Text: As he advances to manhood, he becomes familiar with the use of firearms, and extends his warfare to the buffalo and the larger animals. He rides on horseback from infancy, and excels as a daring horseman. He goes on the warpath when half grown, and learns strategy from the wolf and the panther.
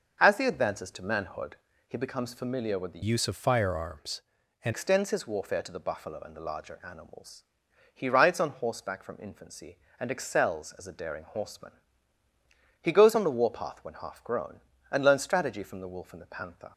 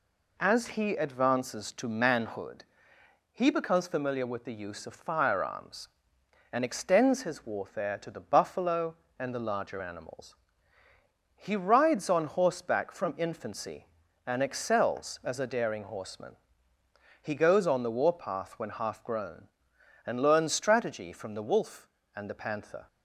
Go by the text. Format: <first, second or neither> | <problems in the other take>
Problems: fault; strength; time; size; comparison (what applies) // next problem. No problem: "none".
second | changes voice from "use" to "and"; from 3.0 to 4.7 s; 1.7 s long